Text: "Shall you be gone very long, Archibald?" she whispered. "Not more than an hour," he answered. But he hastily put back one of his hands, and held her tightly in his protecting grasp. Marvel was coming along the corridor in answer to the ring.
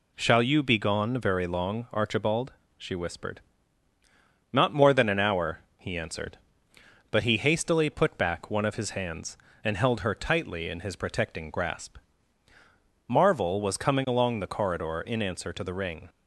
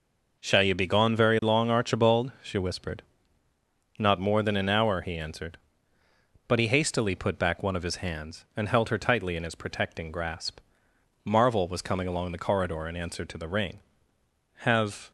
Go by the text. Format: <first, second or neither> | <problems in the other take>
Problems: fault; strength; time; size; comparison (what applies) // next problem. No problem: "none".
first | goes on to say "Have"; from 14.6 s on; 0.50 s long